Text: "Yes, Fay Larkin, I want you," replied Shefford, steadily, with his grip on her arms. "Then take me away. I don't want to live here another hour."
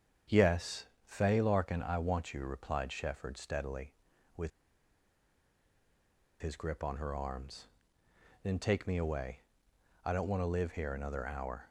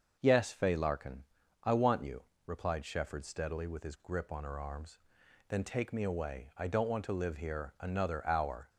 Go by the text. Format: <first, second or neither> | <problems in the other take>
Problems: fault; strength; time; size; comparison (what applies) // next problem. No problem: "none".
second | starts louder than the rest; strong; until 1.5 s; 8 dB; also in the second // pauses between "with" and "his"; strong; at 4.5 s; 1.9 s long